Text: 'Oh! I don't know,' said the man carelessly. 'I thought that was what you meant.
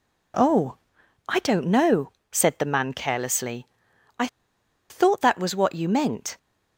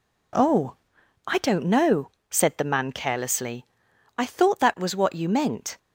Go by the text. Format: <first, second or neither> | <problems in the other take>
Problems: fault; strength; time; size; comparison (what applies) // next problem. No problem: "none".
second | pauses between "I" and "thought"; noticeable; at 4.2 s; 0.62 s long